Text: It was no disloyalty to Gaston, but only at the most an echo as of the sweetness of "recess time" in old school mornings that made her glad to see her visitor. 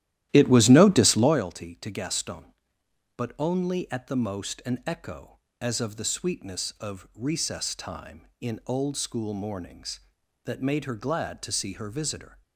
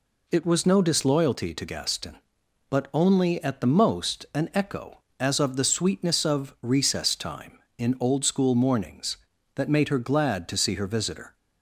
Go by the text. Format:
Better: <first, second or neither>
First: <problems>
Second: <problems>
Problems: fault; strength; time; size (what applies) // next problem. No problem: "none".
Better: second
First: starts louder than the rest; strong; until 1.5 s; 13.5 dB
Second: none